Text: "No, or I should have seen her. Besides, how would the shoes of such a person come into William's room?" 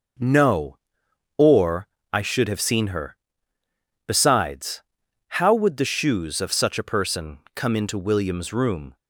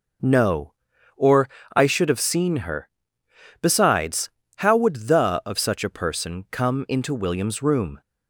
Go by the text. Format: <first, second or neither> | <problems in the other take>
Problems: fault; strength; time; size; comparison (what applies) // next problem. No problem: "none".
first | pauses between "or" and "I"; slight; at 1.4 s; 0.26 s long; slight in the first // skips "shoes"; at 5.4 s